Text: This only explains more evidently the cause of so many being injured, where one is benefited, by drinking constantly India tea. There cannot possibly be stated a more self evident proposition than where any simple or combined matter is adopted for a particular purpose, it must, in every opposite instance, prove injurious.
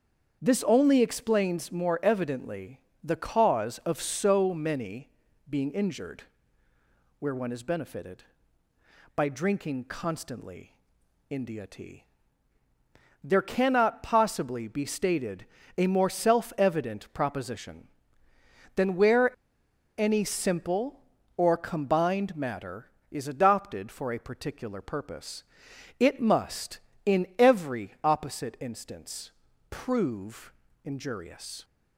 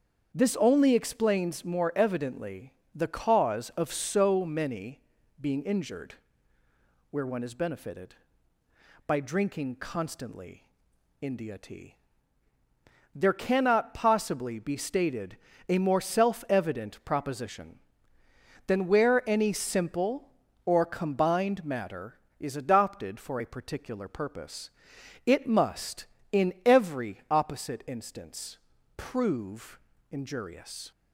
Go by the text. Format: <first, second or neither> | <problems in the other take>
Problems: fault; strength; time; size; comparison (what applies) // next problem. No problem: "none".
second | starts louder than the rest; strong; until 1.4 s; 7.5 dB; strong in the second // pauses between "evidently" and "the"; slight; at 2.7 s; 0.24 s long; slight in the second // pauses between "many" and "being"; at 5.0 s; 0.40 s long; also in the second // pauses between "constantly" and "India"; noticeable; at 10.7 s; 0.54 s long; noticeable in the second // pauses between "stated" and "a"; slight; at 15.4 s; 0.32 s long; slight in the second // pauses between "where" and "any"; noticeable; at 19.3 s; 0.65 s long // pauses between "prove" and "injurious"; slight; at 30.5 s; 0.32 s long; slight in the second